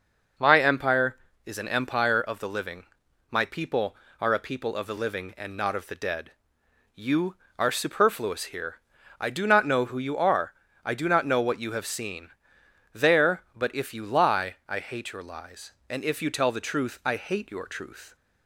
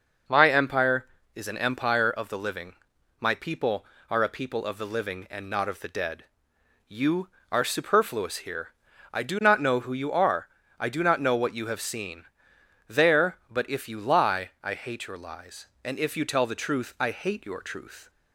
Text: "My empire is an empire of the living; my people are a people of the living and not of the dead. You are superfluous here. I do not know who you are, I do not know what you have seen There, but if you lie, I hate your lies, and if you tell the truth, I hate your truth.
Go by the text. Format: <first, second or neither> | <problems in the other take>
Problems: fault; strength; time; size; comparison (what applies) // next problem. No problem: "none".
neither | pauses between "seen" and "There"; noticeable; the same in both